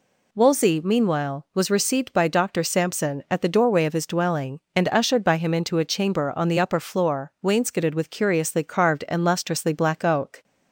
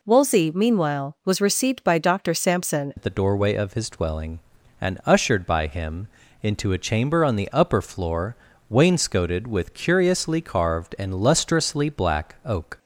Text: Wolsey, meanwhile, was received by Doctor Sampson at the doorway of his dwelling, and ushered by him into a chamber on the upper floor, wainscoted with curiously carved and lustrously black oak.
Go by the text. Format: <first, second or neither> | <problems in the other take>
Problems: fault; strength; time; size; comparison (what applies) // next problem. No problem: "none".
first | changes voice at "at"; from 2.9 s on; 9.8 s long // pauses between "him" and "into"; slight; at 6.0 s; 0.34 s long